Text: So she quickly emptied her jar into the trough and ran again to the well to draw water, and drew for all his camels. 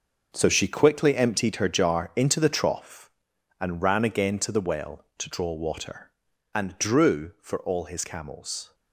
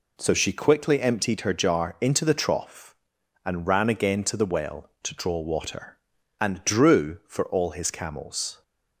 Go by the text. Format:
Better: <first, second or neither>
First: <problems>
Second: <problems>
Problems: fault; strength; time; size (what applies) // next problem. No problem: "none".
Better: second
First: gets quieter; strong; throughout; 12 dB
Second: none